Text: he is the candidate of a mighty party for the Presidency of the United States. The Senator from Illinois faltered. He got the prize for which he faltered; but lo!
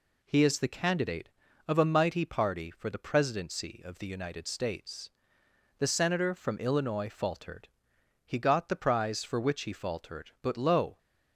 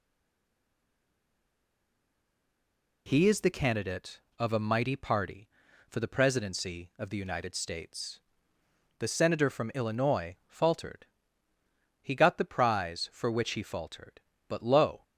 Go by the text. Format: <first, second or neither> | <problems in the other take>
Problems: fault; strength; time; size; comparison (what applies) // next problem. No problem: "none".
first | stays silent before the first word; strong; until 3.0 s; 3.0 s long